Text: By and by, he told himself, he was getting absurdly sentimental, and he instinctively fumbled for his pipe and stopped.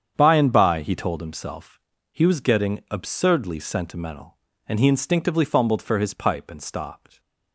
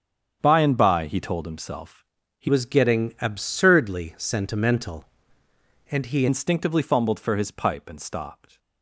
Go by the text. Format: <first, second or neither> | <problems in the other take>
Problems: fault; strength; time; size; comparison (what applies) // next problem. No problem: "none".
first | starts louder than the rest; strong; until 1.4 s; 8 dB; strong in the first // changes voice from "was" to "he"; from 2.4 to 6.2 s; 3.8 s long